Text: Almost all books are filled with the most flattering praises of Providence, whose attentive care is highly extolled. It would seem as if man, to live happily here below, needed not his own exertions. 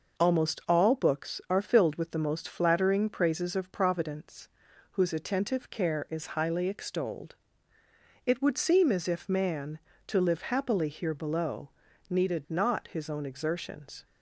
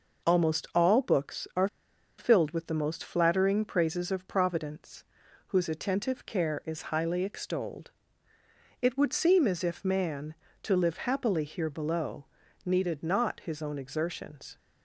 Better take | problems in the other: first | pauses between "are" and "filled"; noticeable; at 1.6 s; 0.52 s long

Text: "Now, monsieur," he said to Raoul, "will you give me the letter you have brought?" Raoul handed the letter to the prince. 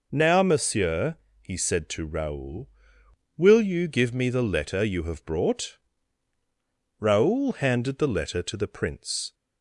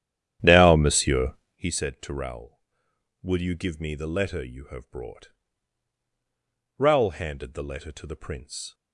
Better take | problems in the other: first | starts louder than the rest; strong; until 1.7 s; 10.5 dB

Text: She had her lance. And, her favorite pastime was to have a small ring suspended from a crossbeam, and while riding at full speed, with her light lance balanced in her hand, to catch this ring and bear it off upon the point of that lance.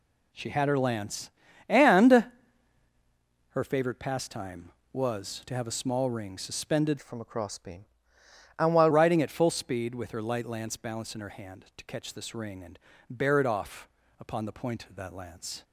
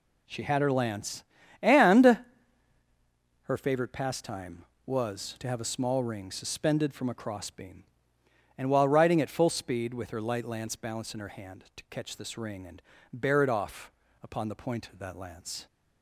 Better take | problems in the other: second | changes voice from "from" to "while"; from 7.0 to 8.9 s; 1.9 s long // pauses between "and" and "bear"; slight; at 12.7 s; 0.30 s long; slight in the second // pauses between "off" and "upon"; slight; at 13.8 s; 0.32 s long; slight in the second

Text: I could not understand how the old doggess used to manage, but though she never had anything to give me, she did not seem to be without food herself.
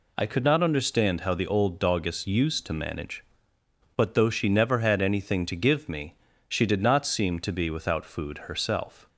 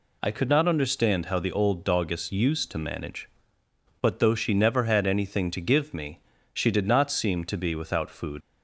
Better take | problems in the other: first | stops before "herself"; at 8.4 s

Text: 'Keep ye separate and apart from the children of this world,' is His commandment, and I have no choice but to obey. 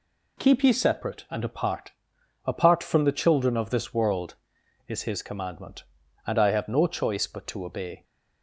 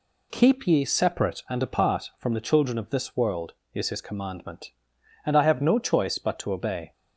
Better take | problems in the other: second | says "apart" twice; at 2.4 s

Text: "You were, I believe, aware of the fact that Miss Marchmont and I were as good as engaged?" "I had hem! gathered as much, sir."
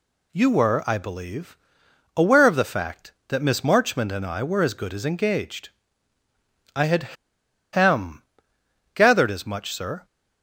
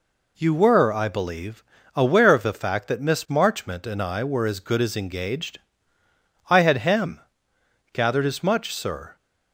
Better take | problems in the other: second | pauses between "had" and "hem"; noticeable; at 7.1 s; 0.59 s long

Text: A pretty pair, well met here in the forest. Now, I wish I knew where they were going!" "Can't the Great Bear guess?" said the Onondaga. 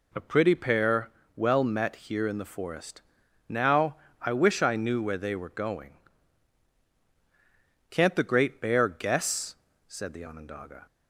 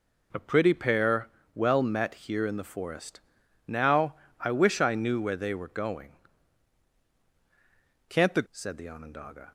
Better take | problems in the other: first | skips "Great Bear guess"; at 8.4 s

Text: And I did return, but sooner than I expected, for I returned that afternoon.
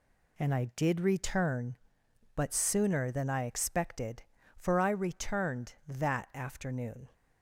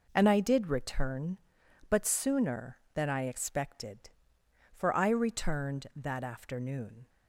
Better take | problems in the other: neither | none

